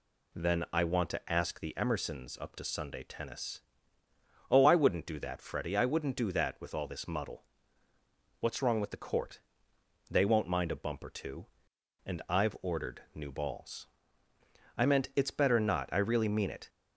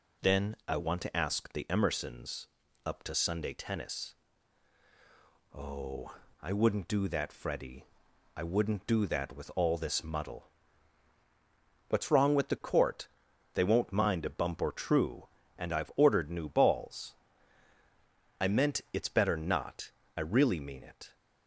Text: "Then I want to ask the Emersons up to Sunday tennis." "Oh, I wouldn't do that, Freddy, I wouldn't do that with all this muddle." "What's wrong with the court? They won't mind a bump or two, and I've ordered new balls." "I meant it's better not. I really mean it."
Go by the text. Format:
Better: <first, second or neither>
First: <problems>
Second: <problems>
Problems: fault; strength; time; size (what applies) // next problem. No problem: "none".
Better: first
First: none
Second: pauses between "Emersons" and "up"; at 2.4 s; 0.38 s long // says "true" for "two"; at 14.7 s